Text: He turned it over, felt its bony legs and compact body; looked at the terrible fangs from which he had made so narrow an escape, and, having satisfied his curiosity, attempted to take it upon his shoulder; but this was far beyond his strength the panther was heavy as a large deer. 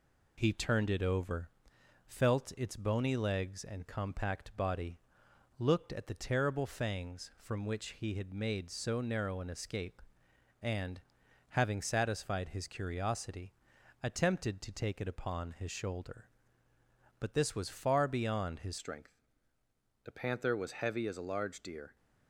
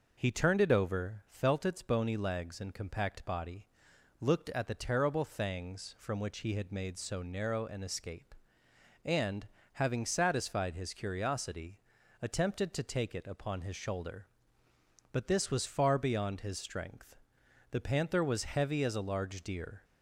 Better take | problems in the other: second | changes voice at "strength"; from 18.7 s on; 3.2 s long // pauses between "strength" and "the"; noticeable; at 19.1 s; 0.88 s long; noticeable in the second

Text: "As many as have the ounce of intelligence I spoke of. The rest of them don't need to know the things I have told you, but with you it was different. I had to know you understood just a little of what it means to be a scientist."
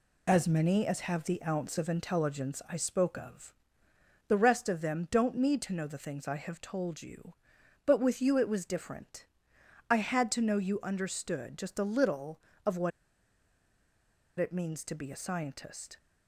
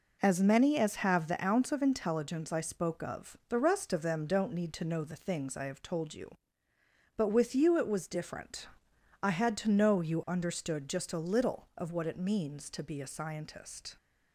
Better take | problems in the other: second | pauses between "what" and "it"; strong; at 12.9 s; 1.4 s long

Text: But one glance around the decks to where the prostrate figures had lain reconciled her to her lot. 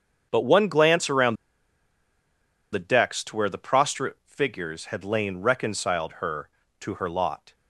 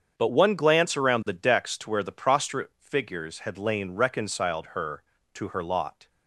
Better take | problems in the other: second | starts louder than the rest; strong; until 1.3 s; 7.5 dB; strong in the second // pauses between "around" and "the"; strong; at 1.3 s; 1.3 s long

